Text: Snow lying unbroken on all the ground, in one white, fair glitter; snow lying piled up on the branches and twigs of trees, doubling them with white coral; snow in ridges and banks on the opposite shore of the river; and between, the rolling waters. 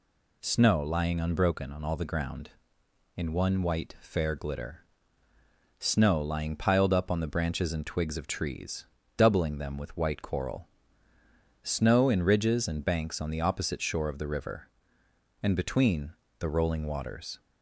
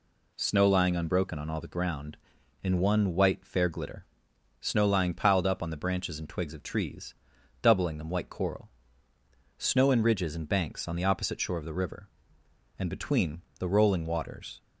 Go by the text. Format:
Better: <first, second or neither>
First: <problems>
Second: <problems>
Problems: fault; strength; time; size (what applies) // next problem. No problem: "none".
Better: first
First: none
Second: skips "with"; at 8.0 s